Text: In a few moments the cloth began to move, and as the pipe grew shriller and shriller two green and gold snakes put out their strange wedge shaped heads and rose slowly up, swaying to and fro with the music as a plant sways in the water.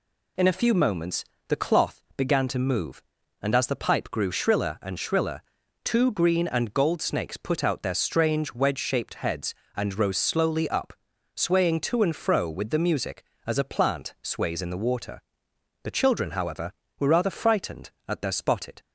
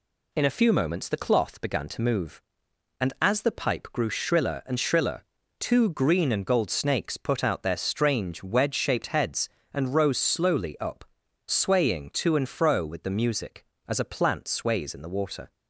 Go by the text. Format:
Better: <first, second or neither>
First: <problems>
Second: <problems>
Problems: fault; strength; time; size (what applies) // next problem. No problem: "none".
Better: second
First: pauses between "moments" and "the"; slight; at 1.2 s; 0.24 s long // pauses between "shriller" and "two"; at 5.4 s; 0.42 s long // goes on to say "The children however were rather frightened at their spotted"; strong; from 15.8 s on; 2.9 s long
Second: pauses between "shriller" and "two"; slight; at 5.2 s; 0.36 s long